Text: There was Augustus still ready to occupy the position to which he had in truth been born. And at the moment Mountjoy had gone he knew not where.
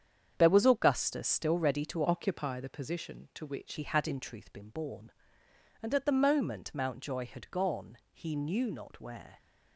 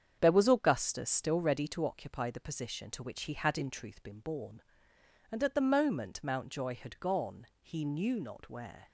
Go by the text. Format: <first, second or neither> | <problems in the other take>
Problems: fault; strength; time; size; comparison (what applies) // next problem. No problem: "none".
second | starts louder than the rest; strong; until 1.3 s; 8 dB; strong in the second // changes voice from "occupy" to "which"; from 2.0 to 3.7 s; 1.7 s long